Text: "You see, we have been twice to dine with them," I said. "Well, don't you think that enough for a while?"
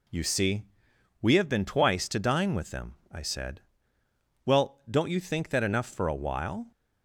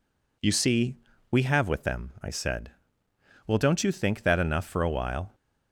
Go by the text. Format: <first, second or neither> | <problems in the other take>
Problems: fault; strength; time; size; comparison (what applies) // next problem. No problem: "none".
first | skips "been twice to dine"; at 1.6 s